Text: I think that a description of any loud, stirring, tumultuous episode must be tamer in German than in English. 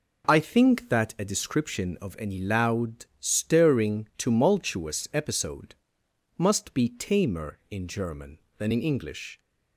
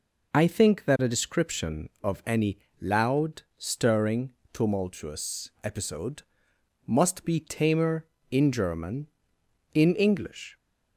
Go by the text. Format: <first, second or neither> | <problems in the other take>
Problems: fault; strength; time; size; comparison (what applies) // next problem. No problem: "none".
first | pauses between "any" and "loud"; slight; at 2.5 s; 0.22 s long // pauses between "episode" and "must"; noticeable; at 6.2 s; 0.64 s long; noticeable in the first // skips "than"; at 9.4 s